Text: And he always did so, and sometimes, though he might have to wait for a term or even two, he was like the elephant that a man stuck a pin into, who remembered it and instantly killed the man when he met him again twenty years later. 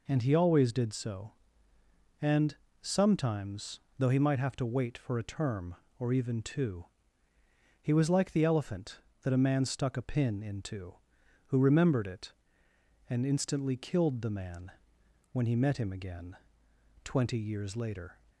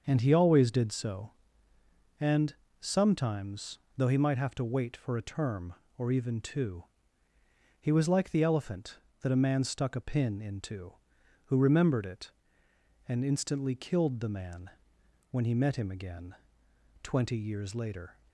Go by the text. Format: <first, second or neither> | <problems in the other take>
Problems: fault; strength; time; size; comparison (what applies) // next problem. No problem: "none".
first | starts louder than the rest; until 1.5 s; 6.5 dB // pauses between "and" and "sometimes"; slight; at 2.5 s; 0.26 s long; slight in the first // pauses between "man" and "when"; noticeable; at 14.7 s; 0.60 s long; noticeable in the first // pauses between "again" and "twenty"; noticeable; at 16.3 s; 0.68 s long; noticeable in the first